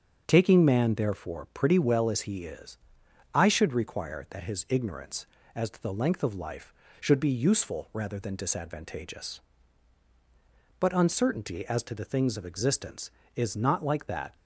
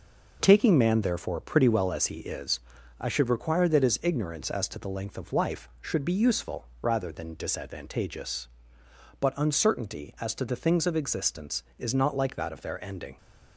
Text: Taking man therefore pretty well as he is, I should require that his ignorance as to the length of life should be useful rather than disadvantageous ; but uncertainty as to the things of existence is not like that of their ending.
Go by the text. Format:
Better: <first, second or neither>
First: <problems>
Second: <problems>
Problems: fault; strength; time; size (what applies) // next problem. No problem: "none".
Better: second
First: starts louder than the rest; strong; until 1.2 s; 7.5 dB // stops before "of their ending"; at 14.3 s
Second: none